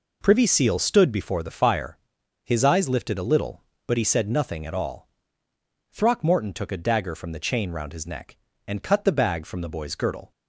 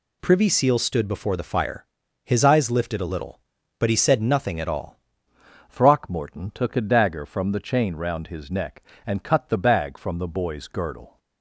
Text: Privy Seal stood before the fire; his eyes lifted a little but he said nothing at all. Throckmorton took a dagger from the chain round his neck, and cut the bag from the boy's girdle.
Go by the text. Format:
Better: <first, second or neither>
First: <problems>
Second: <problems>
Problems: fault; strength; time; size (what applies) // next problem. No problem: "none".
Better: first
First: none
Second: changes voice at "Throckmorton"; from 5.6 s on; 5.5 s long